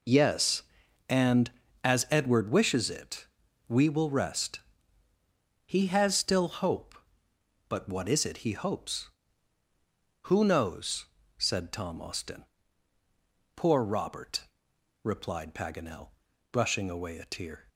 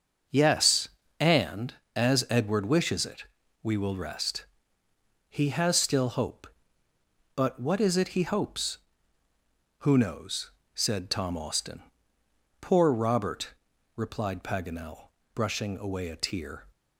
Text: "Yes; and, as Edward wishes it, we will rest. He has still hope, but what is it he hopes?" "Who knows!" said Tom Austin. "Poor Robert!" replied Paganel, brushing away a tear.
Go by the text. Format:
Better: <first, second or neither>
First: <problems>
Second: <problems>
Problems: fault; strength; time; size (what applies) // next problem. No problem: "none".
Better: neither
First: none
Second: none